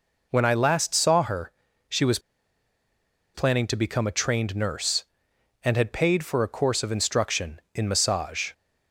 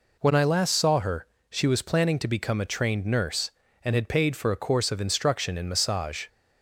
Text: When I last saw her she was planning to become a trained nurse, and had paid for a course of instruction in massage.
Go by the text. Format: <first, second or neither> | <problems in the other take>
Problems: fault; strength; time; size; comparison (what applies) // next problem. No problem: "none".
second | pauses between "her" and "she"; slight; at 1.5 s; 0.36 s long; slight in the second // pauses between "was" and "planning"; at 2.1 s; 1.1 s long